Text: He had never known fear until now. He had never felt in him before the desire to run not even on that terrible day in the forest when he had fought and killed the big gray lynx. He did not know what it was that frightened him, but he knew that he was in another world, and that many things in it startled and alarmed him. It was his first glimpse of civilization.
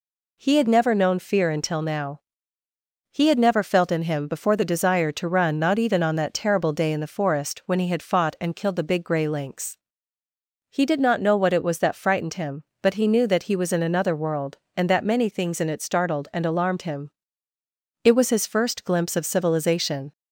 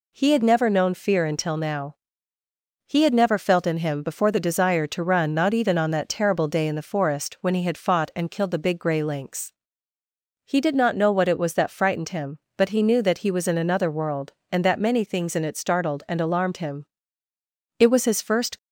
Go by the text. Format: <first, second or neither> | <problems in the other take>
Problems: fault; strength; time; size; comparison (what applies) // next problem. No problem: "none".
first | stops before "glimpse of civilization"; at 18.5 s